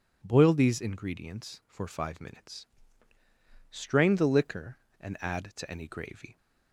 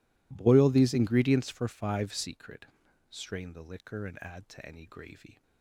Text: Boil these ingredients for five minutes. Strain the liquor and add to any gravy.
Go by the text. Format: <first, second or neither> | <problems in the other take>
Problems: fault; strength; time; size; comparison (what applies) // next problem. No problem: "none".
first | says "secret" for "minutes"; at 2.1 s